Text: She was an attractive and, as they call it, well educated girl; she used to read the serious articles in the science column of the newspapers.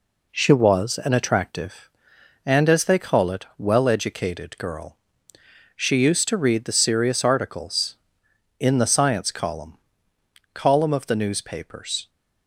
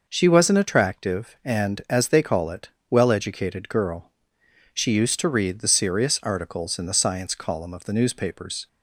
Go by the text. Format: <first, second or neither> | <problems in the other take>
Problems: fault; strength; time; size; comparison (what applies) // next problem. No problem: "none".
second | says "column" twice; at 10.5 s